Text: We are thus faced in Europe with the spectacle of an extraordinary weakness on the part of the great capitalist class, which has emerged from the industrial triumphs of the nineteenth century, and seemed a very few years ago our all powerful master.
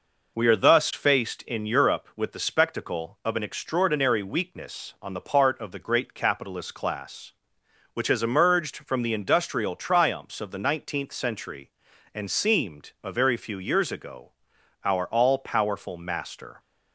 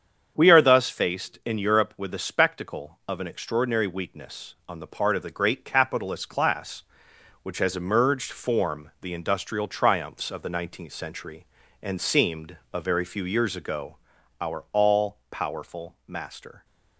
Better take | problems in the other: first | starts louder than the rest; strong; until 1.3 s; 7.5 dB // says "form" for "from"; at 8.3 s // pauses between "seemed" and "a"; slight; at 12.5 s; 0.16 s long // pauses between "ago" and "our"; noticeable; at 13.9 s; 0.46 s long; noticeable in the first

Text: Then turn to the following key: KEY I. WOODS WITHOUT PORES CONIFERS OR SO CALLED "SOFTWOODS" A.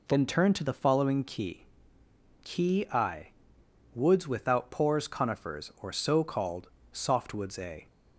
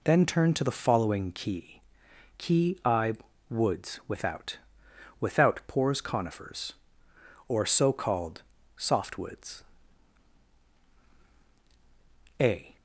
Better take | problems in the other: first | says "WITHOUT" twice; at 5.1 s // pauses between "CALLED" and "SOFTWOODS"; slight; at 8.4 s; 0.32 s long; slight in the first // pauses between "SOFTWOODS" and "A"; strong; at 9.6 s; 2.7 s long

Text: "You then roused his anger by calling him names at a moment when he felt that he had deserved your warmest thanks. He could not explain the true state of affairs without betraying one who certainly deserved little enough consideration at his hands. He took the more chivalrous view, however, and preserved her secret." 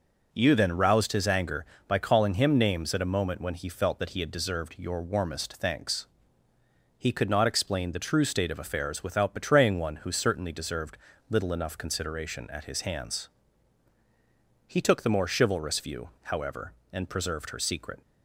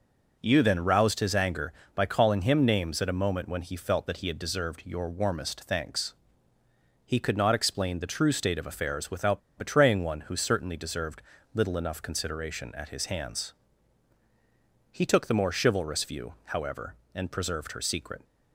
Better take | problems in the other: first | pauses between "without" and "betraying"; slight; at 9.3 s; 0.17 s long // pauses between "deserved" and "little"; slight; at 11.2 s; 0.32 s long; slight in the first

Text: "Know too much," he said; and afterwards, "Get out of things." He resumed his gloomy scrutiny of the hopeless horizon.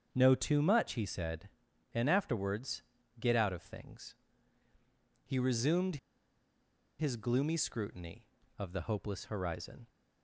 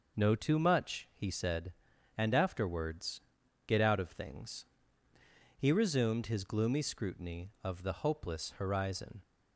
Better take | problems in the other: second | starts louder than the rest; strong; until 1.1 s; 7 dB // pauses between "resumed" and "his"; at 5.9 s; 1.0 s long

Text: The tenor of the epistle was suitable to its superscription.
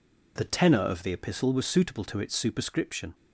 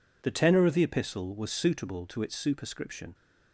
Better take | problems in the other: neither | none

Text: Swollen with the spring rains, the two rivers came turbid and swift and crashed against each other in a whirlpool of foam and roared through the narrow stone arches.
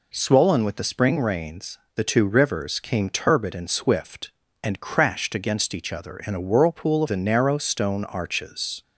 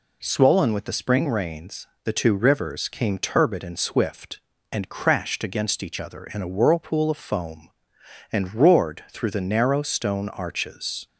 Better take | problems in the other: second | skips "foam and roared through"; at 7.0 s

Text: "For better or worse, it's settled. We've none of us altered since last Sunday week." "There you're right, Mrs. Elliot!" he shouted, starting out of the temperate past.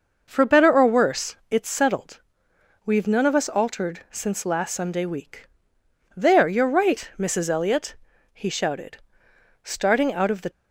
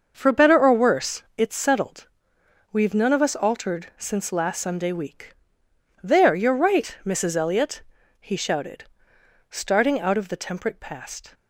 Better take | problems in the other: second | starts louder than the rest; noticeable; until 1.2 s; 6 dB; also in the second // stops before "temperate past"; at 10.5 s

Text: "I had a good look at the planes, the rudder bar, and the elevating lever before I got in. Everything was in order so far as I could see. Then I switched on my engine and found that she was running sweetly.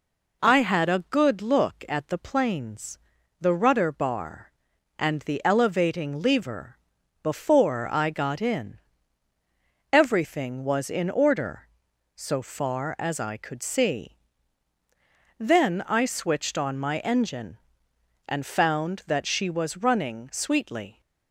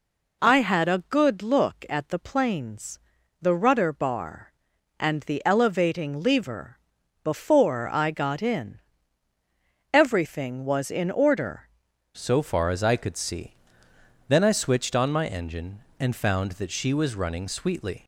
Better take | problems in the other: first | pauses between "lever" and "before"; noticeable; at 6.7 s; 0.46 s long; noticeable in the first // changes voice at "so"; from 12.1 s on; 5.9 s long

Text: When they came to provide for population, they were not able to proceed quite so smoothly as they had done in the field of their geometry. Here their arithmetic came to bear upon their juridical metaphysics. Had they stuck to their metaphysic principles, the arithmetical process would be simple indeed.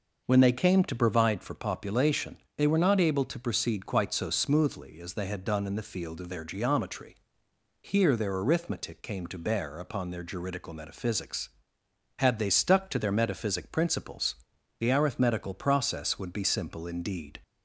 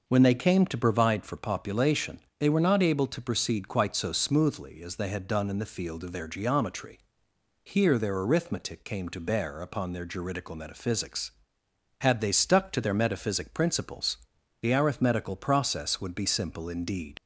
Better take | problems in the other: first | leaves "indeed" unfinished; at 17.1 s; 65 ms

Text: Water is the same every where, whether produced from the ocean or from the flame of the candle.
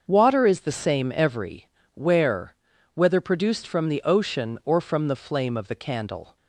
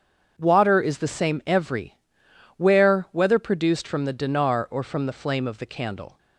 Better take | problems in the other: first | starts louder than the rest; strong; until 1.4 s; 7 dB; also in the first // pauses between "every" and "where"; noticeable; at 1.9 s; 0.62 s long; slight in the first // says "dinar" for "ocean"; at 4.1 s

